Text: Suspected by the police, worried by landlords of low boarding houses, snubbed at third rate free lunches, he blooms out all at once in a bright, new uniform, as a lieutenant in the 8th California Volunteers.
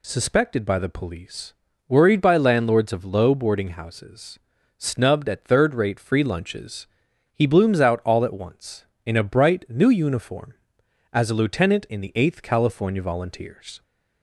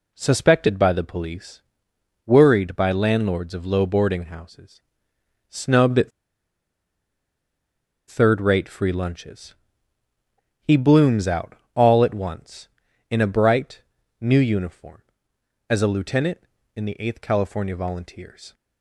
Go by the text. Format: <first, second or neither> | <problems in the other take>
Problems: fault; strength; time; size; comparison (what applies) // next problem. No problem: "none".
first | pauses between "at" and "third"; strong; at 6.1 s; 1.9 s long // pauses between "out" and "all"; slight; at 11.5 s; 0.20 s long